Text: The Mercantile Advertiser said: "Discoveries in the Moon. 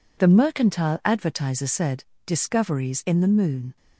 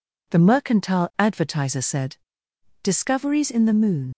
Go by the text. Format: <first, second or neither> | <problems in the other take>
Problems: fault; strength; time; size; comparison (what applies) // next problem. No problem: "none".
first | leaves "Moon" unfinished; at 4.1 s; 65 ms